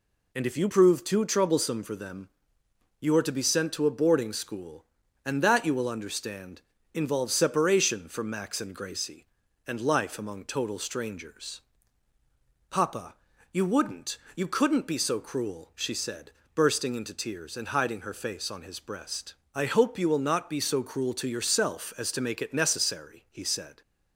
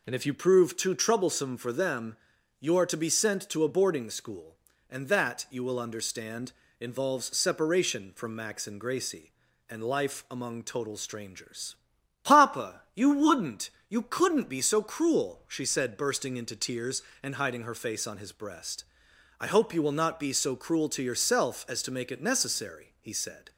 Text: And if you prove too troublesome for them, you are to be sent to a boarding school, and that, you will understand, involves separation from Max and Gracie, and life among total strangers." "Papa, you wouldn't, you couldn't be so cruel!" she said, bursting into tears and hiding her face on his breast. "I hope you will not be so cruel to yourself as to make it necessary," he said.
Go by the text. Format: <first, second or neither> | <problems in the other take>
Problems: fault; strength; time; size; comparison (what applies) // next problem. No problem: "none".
neither | none